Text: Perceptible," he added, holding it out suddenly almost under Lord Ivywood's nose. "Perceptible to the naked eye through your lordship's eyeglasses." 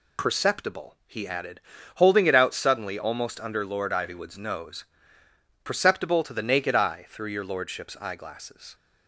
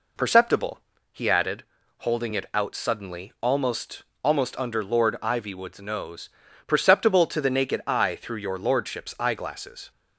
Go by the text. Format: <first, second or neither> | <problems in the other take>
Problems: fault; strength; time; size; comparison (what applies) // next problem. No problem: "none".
first | says "almost" twice; at 4.2 s